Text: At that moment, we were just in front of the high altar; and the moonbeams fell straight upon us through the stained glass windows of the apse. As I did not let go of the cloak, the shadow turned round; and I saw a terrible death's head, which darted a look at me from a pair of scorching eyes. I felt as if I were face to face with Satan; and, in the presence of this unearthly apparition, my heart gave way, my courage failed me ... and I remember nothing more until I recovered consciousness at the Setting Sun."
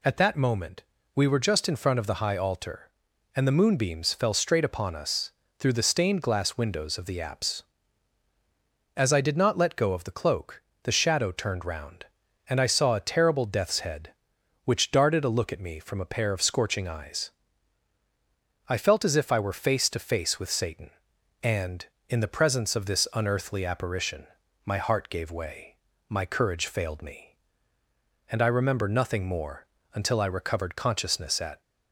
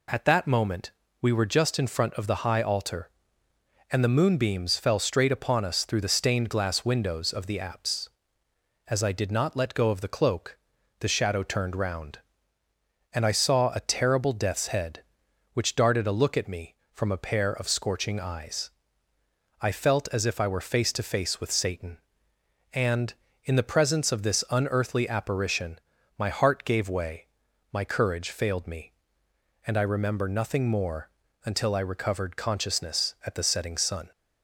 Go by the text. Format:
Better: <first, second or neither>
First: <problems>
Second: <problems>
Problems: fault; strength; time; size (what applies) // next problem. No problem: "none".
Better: second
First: pauses between "us" and "through"; slight; at 5.3 s; 0.26 s long // pauses between "more" and "until"; slight; at 29.6 s; 0.30 s long // stops before "the Setting Sun"; at 31.6 s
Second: pauses between "more" and "until"; slight; at 31.0 s; 0.34 s long